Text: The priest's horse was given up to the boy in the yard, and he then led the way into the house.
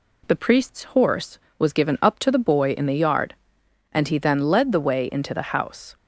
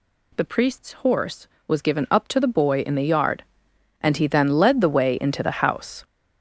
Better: first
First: none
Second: gets louder; strong; throughout; 10.5 dB

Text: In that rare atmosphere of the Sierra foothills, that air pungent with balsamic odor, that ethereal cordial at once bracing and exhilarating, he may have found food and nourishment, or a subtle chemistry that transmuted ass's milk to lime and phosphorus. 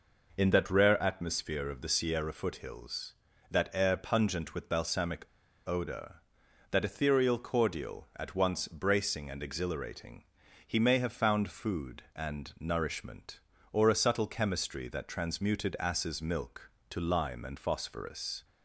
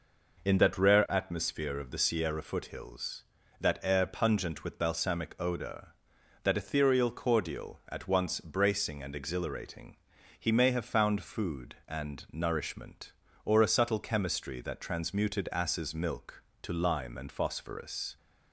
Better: second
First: pauses between "balsamic" and "odor"; at 5.2 s; 0.41 s long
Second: none

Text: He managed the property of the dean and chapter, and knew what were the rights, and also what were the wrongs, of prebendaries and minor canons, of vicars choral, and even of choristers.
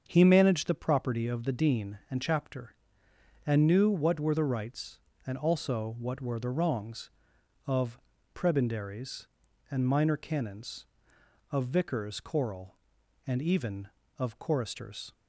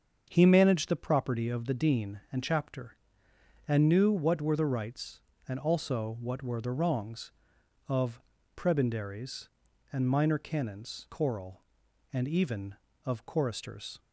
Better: first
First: starts louder than the rest; until 1.0 s; 7 dB // pauses between "of" and "prebendaries"; slight; at 7.9 s; 0.34 s long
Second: starts louder than the rest; until 1.2 s; 7 dB // pauses between "of" and "prebendaries"; slight; at 8.2 s; 0.34 s long // skips "of vicars"; at 11.0 s

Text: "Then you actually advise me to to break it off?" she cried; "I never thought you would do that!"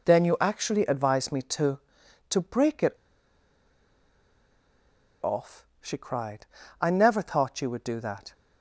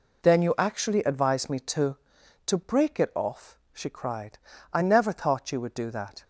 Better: second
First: pauses between "it" and "off"; strong; at 2.9 s; 2.2 s long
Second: none

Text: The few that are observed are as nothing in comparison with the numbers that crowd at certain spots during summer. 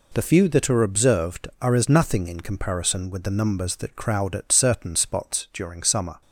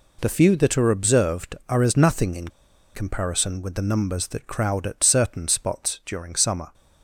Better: first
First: none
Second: pauses between "in" and "comparison"; at 2.4 s; 0.44 s long

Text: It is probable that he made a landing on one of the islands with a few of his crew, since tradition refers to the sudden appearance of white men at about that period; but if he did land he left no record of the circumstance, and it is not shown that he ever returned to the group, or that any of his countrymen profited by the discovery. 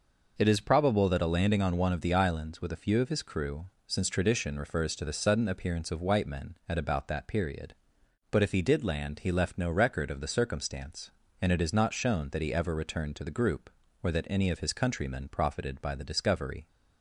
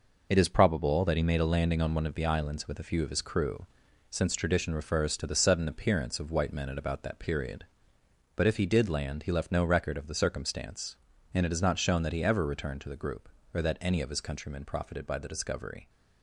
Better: second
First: skips "he made"; at 1.2 s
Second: none

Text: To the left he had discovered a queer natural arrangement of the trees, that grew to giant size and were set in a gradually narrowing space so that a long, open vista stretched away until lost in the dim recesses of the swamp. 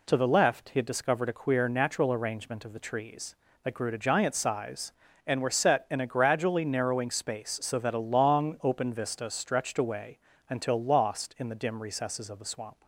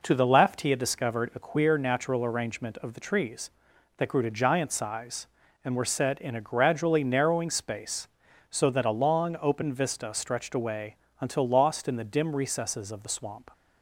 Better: neither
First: pauses between "away" and "until"; slight; at 10.1 s; 0.28 s long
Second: pauses between "away" and "until"; slight; at 10.9 s; 0.24 s long

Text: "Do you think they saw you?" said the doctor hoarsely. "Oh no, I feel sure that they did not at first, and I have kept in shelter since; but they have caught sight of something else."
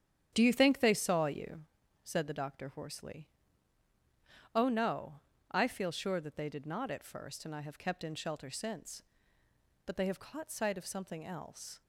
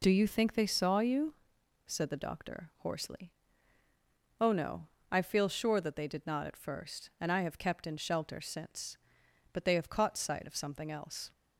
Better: second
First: starts louder than the rest; strong; until 1.8 s; 9.5 dB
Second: none

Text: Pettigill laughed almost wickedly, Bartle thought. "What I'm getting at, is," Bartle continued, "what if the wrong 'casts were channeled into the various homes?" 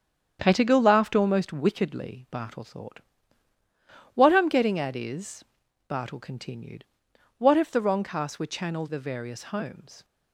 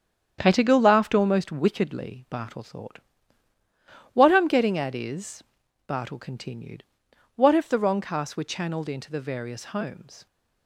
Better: second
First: starts louder than the rest; strong; until 1.4 s; 8.5 dB // skips "into"; at 8.8 s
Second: starts louder than the rest; strong; until 1.4 s; 8.5 dB

